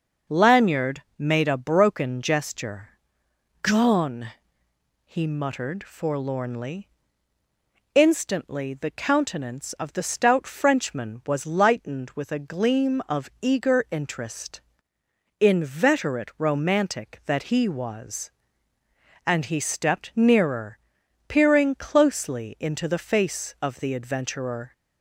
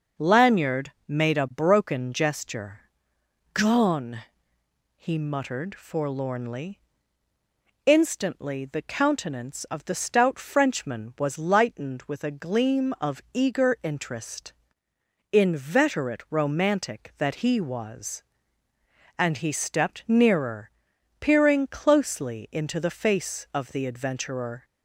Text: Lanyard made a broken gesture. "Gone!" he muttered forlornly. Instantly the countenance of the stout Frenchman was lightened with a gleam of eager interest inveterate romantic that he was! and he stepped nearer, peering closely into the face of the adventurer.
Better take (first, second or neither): neither